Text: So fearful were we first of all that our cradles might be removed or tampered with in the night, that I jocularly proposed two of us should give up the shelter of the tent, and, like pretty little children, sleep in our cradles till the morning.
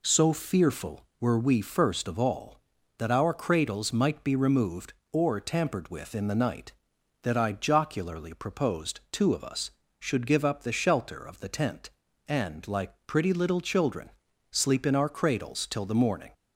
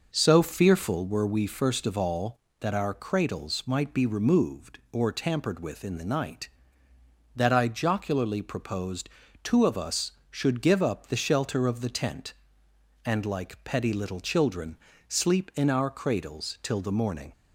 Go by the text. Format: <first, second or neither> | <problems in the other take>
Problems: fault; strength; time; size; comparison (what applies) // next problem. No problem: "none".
first | pauses between "proposed" and "two"; slight; at 9.0 s; 0.34 s long // says "petty" for "pretty"; at 13.6 s